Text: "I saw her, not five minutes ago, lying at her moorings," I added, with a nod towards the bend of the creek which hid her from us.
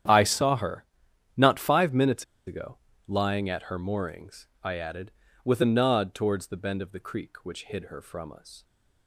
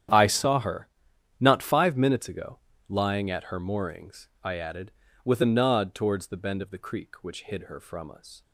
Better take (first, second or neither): second